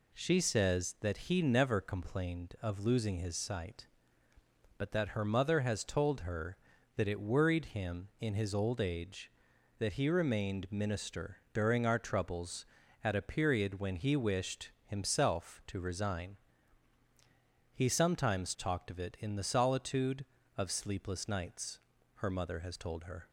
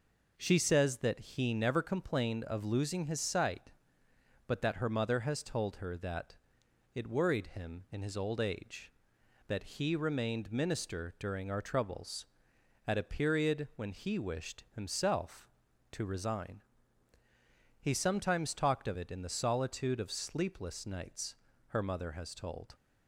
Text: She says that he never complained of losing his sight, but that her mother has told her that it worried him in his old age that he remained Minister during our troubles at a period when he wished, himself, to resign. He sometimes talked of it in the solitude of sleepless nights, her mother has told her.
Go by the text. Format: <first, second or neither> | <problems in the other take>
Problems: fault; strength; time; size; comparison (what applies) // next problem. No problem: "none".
first | pauses between "that" and "it"; noticeable; at 6.3 s; 0.56 s long // stops before "her"; at 22.7 s